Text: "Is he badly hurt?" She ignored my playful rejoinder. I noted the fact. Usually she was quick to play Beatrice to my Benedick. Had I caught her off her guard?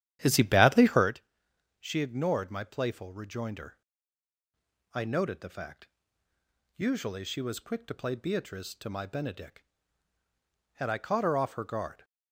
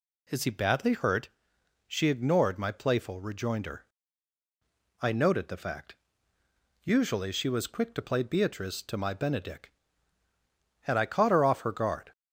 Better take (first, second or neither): second